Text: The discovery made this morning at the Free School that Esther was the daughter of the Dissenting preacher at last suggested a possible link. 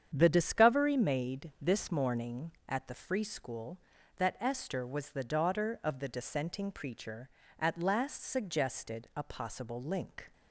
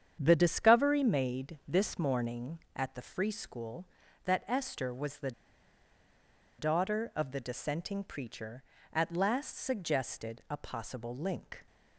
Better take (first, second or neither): first